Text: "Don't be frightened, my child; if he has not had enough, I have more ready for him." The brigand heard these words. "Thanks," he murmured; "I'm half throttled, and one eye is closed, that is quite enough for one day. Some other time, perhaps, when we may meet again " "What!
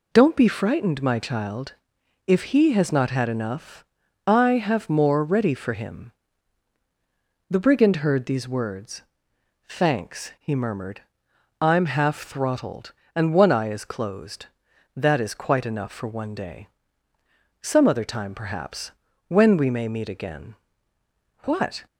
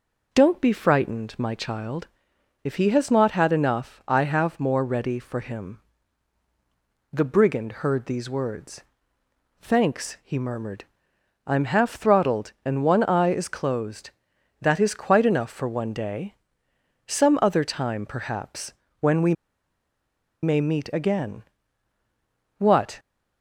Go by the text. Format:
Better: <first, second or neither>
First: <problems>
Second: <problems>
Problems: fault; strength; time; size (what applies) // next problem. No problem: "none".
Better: first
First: none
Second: pauses between "we" and "may"; at 19.3 s; 1.0 s long